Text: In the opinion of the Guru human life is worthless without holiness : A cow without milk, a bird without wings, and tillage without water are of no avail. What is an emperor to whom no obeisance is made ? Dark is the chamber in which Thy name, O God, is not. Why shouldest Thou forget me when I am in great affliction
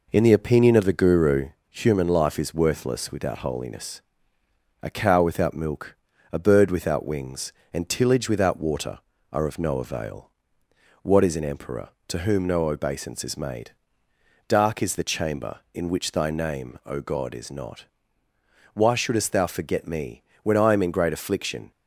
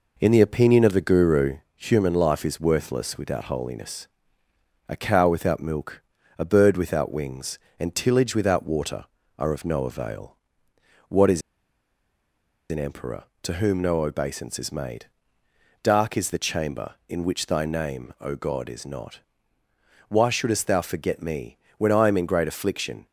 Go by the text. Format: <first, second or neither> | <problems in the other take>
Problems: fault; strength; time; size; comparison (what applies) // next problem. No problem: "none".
first | pauses between "Guru" and "human"; slight; at 1.5 s; 0.16 s long; slight in the first // pauses between "is" and "an"; strong; at 11.4 s; 1.3 s long // pauses between "me" and "when"; slight; at 21.5 s; 0.18 s long; slight in the first